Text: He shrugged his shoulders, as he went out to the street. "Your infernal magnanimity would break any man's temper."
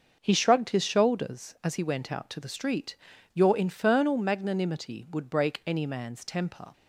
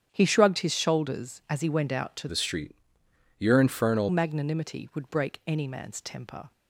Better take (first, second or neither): first